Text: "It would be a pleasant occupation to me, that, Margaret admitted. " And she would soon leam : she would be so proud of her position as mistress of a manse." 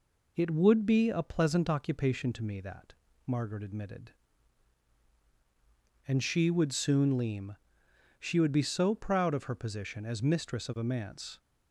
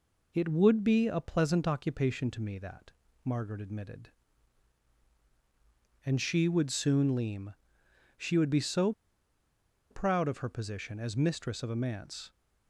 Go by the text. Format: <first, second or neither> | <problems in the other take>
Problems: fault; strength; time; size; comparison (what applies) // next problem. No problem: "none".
first | pauses between "so" and "proud"; noticeable; at 8.9 s; 0.97 s long